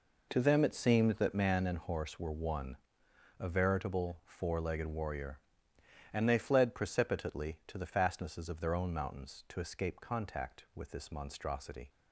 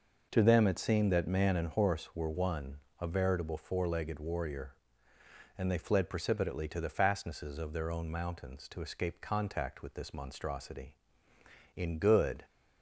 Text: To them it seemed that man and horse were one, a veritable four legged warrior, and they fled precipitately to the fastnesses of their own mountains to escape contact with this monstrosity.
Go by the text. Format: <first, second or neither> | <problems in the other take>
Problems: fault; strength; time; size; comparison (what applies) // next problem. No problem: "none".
first | goes on to say "In good"; noticeable; from 11.7 s on; 0.70 s long